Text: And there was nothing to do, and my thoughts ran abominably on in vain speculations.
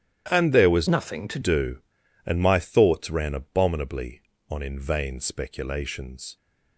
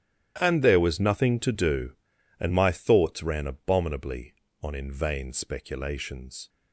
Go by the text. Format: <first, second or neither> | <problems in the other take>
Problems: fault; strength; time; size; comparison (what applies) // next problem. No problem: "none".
second | starts louder than the rest; strong; until 1.2 s; 11 dB; strong in the second // changes voice from "nothing" to "to"; from 0.8 to 1.3 s; 0.5 s long